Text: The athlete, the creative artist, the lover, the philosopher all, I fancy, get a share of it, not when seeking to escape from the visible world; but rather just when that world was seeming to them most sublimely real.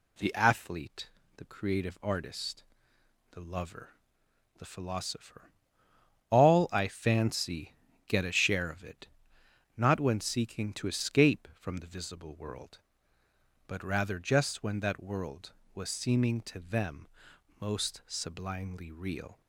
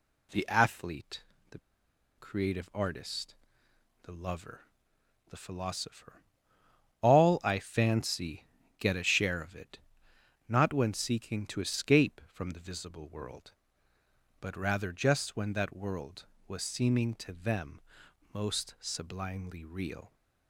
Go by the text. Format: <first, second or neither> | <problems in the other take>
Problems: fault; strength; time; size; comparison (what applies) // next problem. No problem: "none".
first | pauses between "the" and "creative"; noticeable; at 1.5 s; 0.59 s long // pauses between "philosopher" and "all"; noticeable; at 6.2 s; 0.78 s long; noticeable in the first // pauses between "them" and "most"; noticeable; at 17.8 s; 0.50 s long; noticeable in the first